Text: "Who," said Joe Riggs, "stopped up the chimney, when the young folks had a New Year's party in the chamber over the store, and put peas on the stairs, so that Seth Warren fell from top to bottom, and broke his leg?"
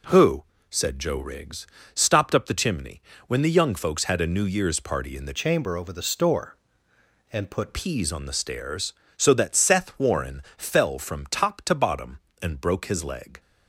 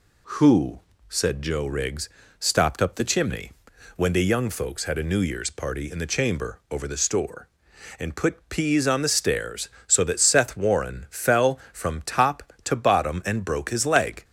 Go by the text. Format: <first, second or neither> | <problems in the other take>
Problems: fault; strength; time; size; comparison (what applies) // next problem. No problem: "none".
second | changes voice from "chamber" to "put"; from 5.3 to 7.7 s; 2.4 s long // pauses between "Warren" and "fell"; slight; at 10.4 s; 0.16 s long